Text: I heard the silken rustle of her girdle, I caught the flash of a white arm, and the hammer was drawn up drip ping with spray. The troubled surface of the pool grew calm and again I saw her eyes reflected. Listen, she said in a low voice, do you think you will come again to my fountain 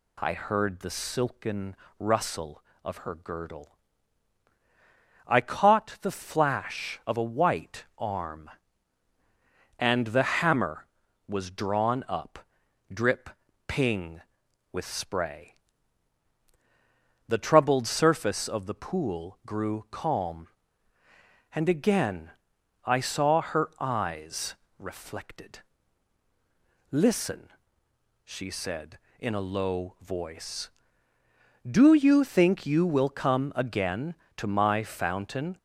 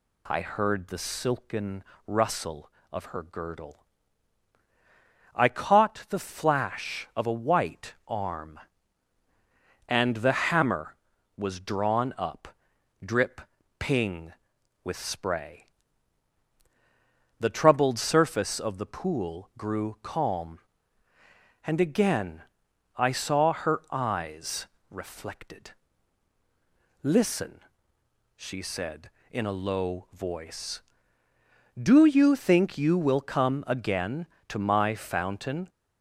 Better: neither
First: pauses between "silken" and "rustle"; slight; at 1.7 s; 0.24 s long // pauses between "white" and "arm"; slight; at 7.8 s; 0.16 s long // pauses between "up" and "drip"; noticeable; at 12.3 s; 0.54 s long // pauses between "drip" and "ping"; at 13.2 s; 0.38 s long // pauses between "again" and "I"; noticeable; at 22.3 s; 0.54 s long // pauses between "eyes" and "reflected"; slight; at 24.5 s; 0.24 s long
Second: pauses between "silken" and "rustle"; slight; at 1.8 s; 0.24 s long // pauses between "white" and "arm"; slight; at 7.9 s; 0.16 s long // pauses between "up" and "drip"; noticeable; at 12.4 s; 0.56 s long // pauses between "drip" and "ping"; at 13.4 s; 0.38 s long // pauses between "again" and "I"; noticeable; at 22.4 s; 0.54 s long // pauses between "eyes" and "reflected"; slight; at 24.6 s; 0.24 s long

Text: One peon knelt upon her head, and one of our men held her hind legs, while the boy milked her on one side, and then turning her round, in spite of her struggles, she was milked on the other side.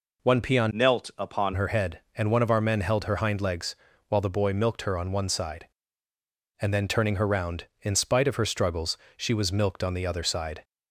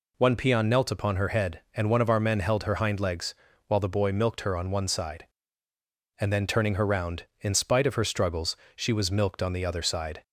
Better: second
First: changes voice from "knelt" to "upon"; from 0.7 to 1.5 s; 0.8 s long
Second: none

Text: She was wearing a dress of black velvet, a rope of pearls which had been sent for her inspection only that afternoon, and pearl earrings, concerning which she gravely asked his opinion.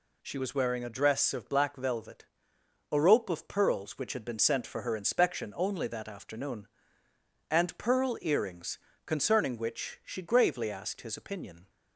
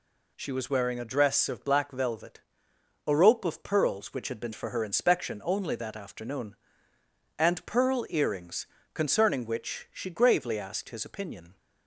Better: first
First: none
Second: skips "sent"; at 4.5 s

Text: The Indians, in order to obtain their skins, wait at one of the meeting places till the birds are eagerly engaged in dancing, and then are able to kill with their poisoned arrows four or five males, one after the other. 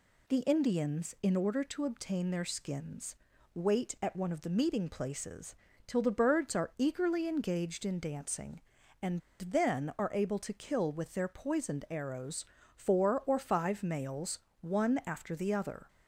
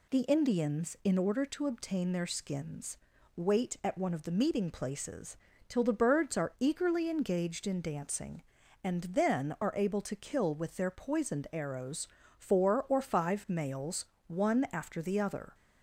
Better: second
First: pauses between "places" and "till"; slight; at 5.5 s; 0.32 s long // pauses between "and" and "then"; slight; at 9.2 s; 0.19 s long // pauses between "arrows" and "four"; slight; at 12.4 s; 0.30 s long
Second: pauses between "places" and "till"; slight; at 5.3 s; 0.32 s long // pauses between "arrows" and "four"; slight; at 12.0 s; 0.30 s long

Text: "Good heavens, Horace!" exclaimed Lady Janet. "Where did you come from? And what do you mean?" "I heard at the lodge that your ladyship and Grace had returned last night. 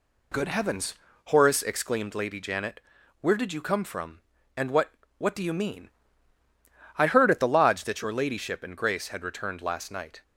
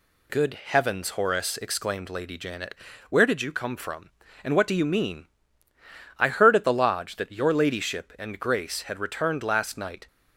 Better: second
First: says "what" twice; at 5.1 s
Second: none

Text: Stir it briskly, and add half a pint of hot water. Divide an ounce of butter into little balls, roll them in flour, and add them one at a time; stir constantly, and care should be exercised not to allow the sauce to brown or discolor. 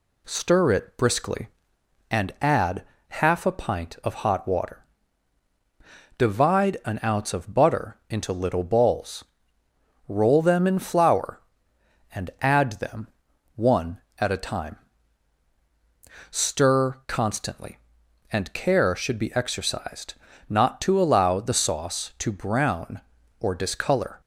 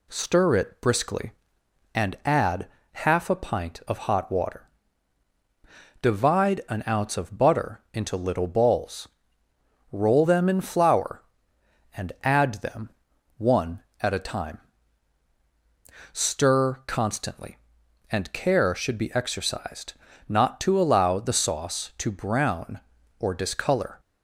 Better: neither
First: pauses between "add" and "half"; slight; at 2.8 s; 0.26 s long // pauses between "them" and "one"; noticeable; at 13.0 s; 0.46 s long // pauses between "exercised" and "not"; slight; at 20.1 s; 0.34 s long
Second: pauses between "add" and "half"; slight; at 2.6 s; 0.26 s long // pauses between "them" and "one"; noticeable; at 12.8 s; 0.46 s long // pauses between "exercised" and "not"; slight; at 19.9 s; 0.34 s long

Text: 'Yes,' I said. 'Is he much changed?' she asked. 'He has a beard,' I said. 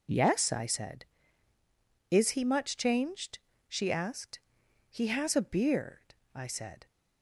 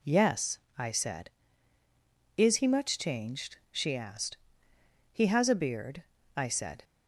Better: neither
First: none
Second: none

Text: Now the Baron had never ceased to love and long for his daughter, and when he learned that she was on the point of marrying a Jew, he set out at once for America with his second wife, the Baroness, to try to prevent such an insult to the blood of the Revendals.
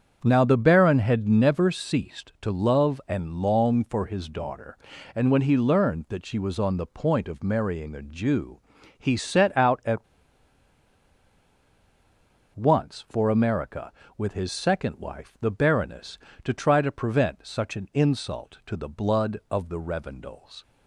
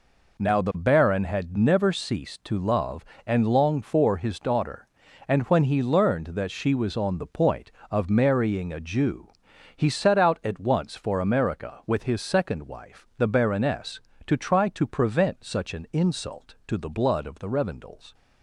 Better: second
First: starts louder than the rest; strong; until 1.2 s; 7.5 dB // pauses between "at" and "once"; strong; at 10.0 s; 2.5 s long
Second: none

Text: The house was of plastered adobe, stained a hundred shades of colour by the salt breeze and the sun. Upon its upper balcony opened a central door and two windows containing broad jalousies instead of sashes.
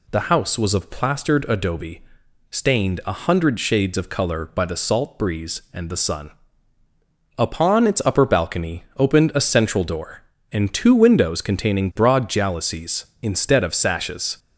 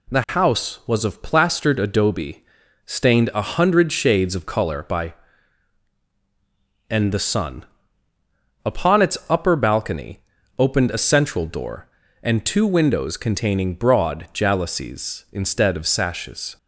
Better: first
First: none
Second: skips "the salt breeze"; at 6.0 s // pauses between "balcony" and "opened"; at 10.1 s; 0.40 s long

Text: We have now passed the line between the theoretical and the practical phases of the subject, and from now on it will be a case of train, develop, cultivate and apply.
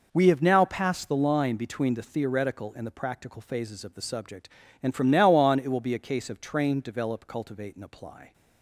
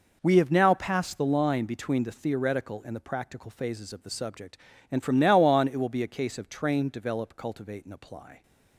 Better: neither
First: none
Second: none

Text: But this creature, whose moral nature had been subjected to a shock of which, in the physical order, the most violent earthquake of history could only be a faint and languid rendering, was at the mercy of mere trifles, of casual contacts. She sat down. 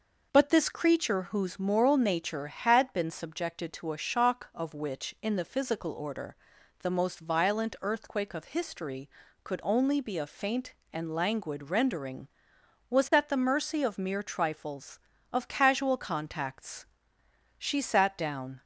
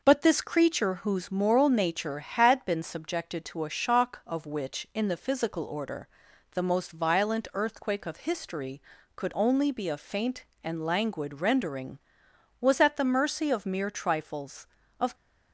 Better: first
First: none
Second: stops before "casual contacts She sat down"; at 15.1 s

